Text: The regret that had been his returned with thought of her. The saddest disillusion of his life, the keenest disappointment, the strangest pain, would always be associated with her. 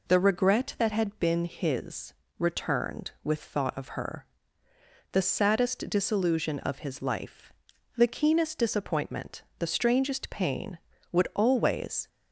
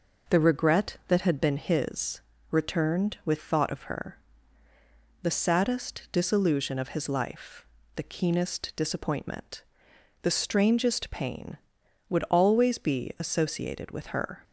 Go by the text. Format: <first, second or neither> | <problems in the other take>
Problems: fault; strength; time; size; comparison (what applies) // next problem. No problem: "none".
second | pauses between "his" and "returned"; slight; at 2.1 s; 0.24 s long; slight in the second // stops before "be associated with her"; at 12.0 s